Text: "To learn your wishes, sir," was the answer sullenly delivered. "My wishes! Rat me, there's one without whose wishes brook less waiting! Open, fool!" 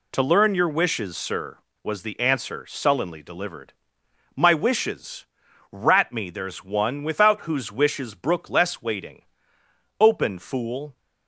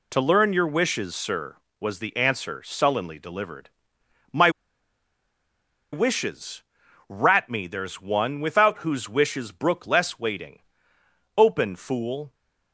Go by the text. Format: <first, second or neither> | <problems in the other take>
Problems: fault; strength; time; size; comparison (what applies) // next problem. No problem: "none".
first | pauses between "My" and "wishes"; strong; at 4.4 s; 1.4 s long